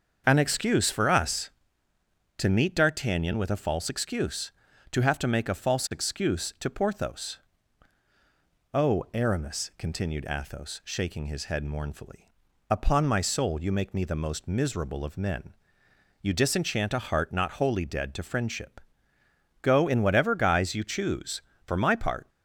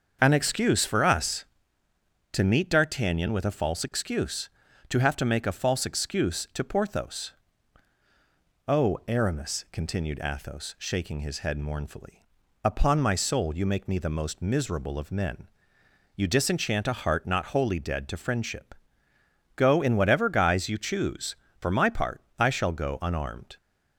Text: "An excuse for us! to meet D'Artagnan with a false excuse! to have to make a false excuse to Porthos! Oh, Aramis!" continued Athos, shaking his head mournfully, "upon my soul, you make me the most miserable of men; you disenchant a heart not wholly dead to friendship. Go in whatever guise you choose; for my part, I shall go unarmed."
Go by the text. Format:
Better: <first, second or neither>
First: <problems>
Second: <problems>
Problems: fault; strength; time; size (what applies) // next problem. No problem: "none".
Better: second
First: starts louder than the rest; until 1.2 s; 6.5 dB // stops before "I shall go unarmed"; at 22.2 s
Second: starts louder than the rest; until 1.2 s; 6.5 dB